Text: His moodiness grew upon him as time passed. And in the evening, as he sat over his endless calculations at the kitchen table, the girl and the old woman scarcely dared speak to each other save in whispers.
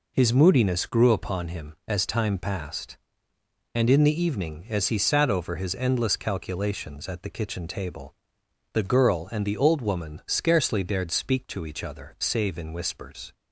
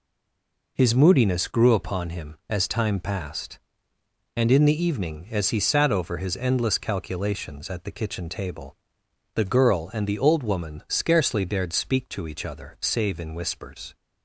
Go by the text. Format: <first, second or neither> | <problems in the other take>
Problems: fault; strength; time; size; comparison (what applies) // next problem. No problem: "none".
first | stays silent before the first word; slight; until 0.7 s; 0.7 s long